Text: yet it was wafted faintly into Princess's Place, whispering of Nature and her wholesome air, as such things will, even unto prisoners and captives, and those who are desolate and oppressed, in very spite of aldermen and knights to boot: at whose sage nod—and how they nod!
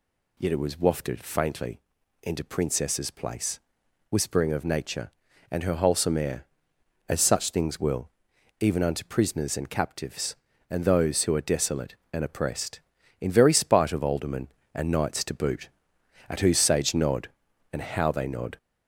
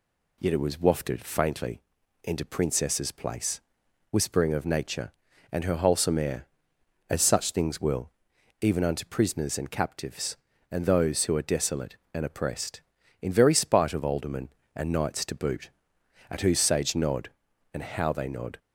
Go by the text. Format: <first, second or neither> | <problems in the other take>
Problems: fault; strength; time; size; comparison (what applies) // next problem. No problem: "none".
second | gets louder; noticeable; throughout; 4 dB // pauses between "faintly" and "into"; at 1.7 s; 0.44 s long; also in the second